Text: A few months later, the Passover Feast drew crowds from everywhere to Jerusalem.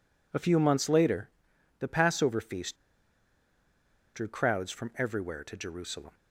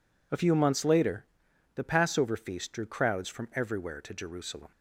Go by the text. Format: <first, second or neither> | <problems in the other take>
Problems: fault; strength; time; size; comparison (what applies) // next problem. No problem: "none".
second | pauses between "Feast" and "drew"; strong; at 2.7 s; 1.3 s long